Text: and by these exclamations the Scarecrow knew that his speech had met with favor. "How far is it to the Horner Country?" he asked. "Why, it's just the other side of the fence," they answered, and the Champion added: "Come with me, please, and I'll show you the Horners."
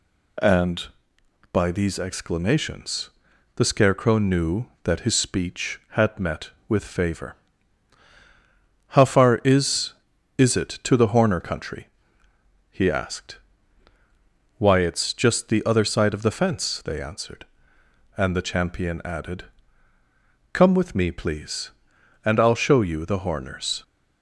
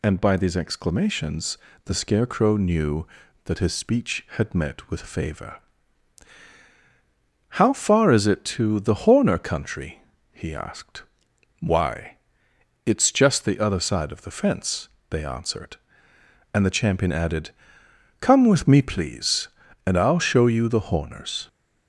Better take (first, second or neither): second